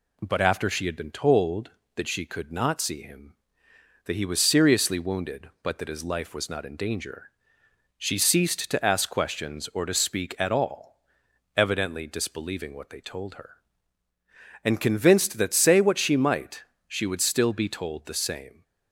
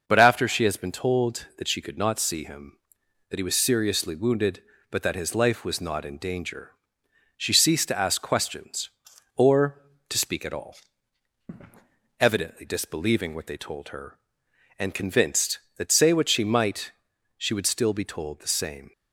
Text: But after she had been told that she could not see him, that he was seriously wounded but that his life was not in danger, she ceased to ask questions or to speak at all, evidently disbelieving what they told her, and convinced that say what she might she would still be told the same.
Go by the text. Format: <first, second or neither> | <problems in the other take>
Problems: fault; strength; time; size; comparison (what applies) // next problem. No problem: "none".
first | says "has" for "had"; at 0.6 s // pauses between "might" and "she"; at 16.9 s; 0.44 s long; slight in the first